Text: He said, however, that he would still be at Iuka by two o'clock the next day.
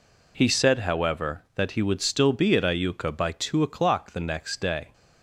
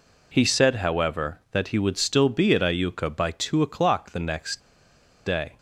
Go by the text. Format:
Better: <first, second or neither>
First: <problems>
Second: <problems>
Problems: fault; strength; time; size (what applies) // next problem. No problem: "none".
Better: first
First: none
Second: pauses between "next" and "day"; noticeable; at 4.6 s; 0.65 s long